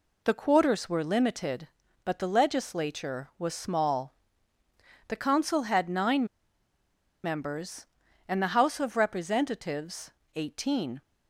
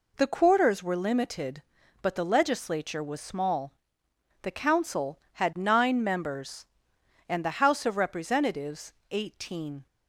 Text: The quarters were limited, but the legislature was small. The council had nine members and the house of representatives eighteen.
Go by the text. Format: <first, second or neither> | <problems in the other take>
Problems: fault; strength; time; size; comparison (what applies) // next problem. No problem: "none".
second | pauses between "nine" and "members"; at 6.2 s; 0.99 s long // pauses between "representatives" and "eighteen"; slight; at 10.1 s; 0.24 s long; slight in the second